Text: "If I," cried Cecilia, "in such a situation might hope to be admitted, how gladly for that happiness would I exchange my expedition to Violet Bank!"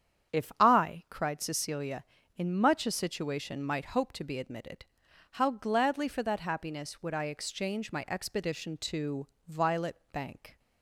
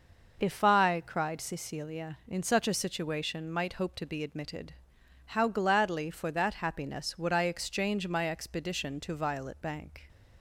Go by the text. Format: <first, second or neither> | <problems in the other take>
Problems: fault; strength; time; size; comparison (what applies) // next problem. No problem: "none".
second | starts louder than the rest; strong; until 1.4 s; 8.5 dB // says "much" for "such"; at 2.5 s // pauses between "to" and "Violet"; slight; at 9.2 s; 0.20 s long